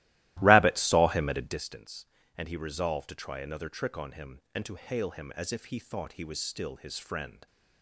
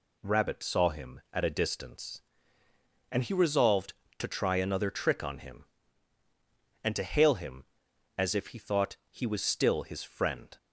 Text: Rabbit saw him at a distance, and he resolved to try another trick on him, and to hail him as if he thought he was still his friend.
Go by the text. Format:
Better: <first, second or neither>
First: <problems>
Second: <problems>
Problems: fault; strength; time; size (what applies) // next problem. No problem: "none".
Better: second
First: starts louder than the rest; strong; until 1.6 s; 16.5 dB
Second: none